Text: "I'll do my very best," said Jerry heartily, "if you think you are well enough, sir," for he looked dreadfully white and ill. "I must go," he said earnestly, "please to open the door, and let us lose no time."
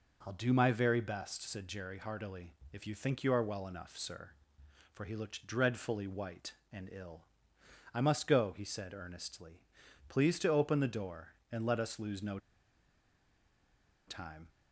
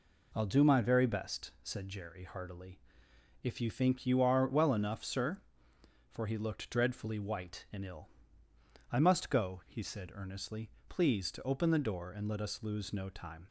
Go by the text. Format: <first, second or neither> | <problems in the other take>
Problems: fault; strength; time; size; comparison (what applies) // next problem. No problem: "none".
second | pauses between "no" and "time"; strong; at 12.3 s; 1.6 s long